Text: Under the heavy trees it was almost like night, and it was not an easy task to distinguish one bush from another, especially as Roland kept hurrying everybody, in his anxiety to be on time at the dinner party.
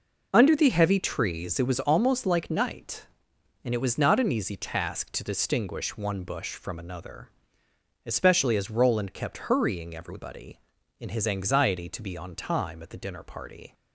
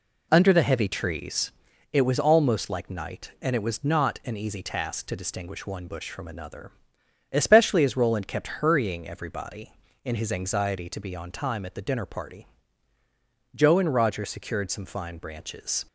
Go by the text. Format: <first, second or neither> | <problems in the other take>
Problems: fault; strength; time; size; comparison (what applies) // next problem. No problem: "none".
first | pauses between "trees" and "it"; at 1.5 s; 0.40 s long // goes on to say "Joe and Roger secured some fine branches"; strong; from 13.5 s on; 2.3 s long